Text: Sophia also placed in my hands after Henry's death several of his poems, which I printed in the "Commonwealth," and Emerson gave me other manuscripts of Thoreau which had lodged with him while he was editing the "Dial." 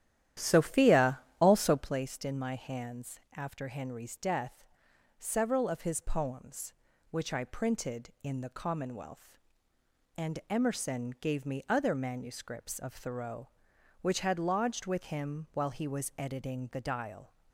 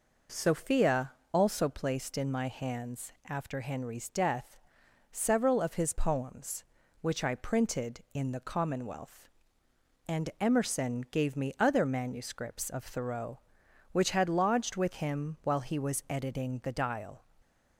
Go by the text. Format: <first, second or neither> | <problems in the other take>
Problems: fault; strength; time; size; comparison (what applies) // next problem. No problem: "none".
second | starts louder than the rest; strong; until 2.0 s; 11.5 dB // pauses between "Sophia" and "also"; slight; at 1.1 s; 0.22 s long; slight in the second // pauses between "hands" and "after"; slight; at 3.1 s; 0.18 s long; slight in the second // pauses between "death" and "several"; noticeable; at 4.6 s; 0.54 s long; noticeable in the second